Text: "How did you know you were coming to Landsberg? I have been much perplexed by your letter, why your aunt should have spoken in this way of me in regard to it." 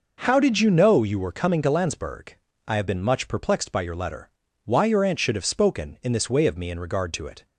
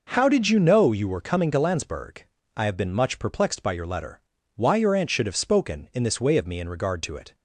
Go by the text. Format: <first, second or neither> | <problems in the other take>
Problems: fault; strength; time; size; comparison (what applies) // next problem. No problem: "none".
neither | none